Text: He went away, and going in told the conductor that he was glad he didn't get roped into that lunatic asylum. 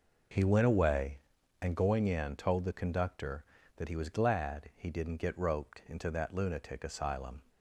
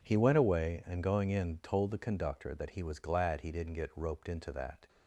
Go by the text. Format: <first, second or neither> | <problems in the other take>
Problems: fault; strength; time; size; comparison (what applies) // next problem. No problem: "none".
first | stops before "lunatic asylum"; at 4.8 s